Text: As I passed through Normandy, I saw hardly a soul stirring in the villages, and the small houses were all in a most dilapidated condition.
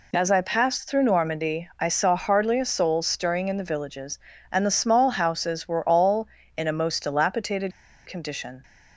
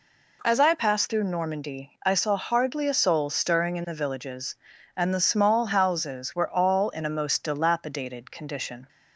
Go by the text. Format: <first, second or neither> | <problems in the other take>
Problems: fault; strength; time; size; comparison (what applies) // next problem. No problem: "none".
second | pauses between "dilapidated" and "condition"; slight; at 7.7 s; 0.34 s long